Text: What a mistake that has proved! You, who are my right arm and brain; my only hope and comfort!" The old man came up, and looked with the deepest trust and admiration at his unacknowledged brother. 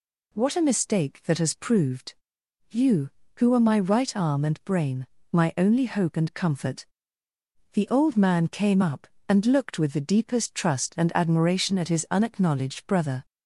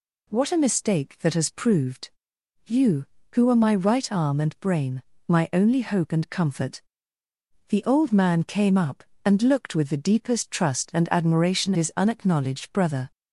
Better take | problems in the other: first | skips "at"; at 11.7 s

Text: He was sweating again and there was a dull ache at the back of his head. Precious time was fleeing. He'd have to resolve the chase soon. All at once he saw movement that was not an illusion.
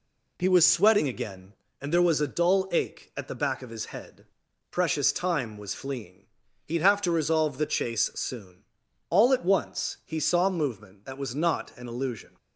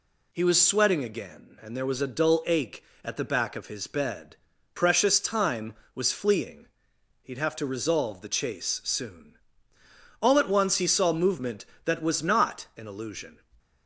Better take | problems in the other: first | says "bed" for "head"; at 3.8 s

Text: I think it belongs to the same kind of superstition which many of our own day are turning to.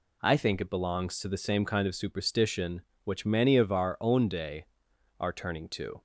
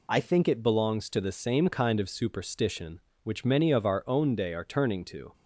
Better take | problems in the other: neither | none

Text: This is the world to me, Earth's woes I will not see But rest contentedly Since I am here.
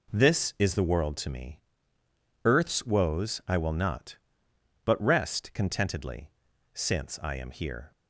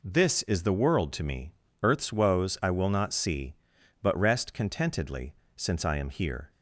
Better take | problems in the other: second | skips "see"; at 4.4 s // pauses between "contentedly" and "Since"; at 6.2 s; 0.44 s long; slight in the second

